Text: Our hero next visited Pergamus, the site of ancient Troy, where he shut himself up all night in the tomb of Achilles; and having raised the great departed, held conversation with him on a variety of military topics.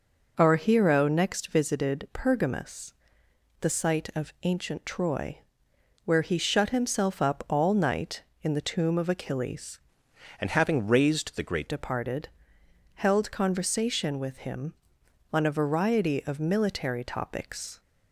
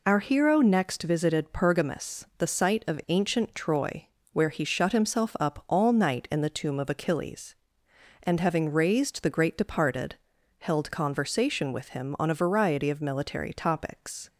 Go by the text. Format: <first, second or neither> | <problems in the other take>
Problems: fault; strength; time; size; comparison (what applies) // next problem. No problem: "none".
second | changes voice from "and" to "great"; from 10.3 to 11.6 s; 1.3 s long